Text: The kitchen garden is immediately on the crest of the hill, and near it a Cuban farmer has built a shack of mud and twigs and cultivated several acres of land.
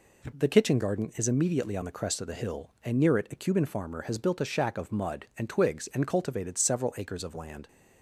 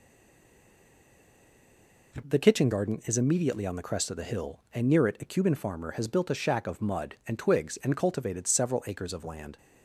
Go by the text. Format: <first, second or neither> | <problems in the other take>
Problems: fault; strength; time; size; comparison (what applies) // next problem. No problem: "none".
first | stays silent before the first word; until 2.1 s; 2.1 s long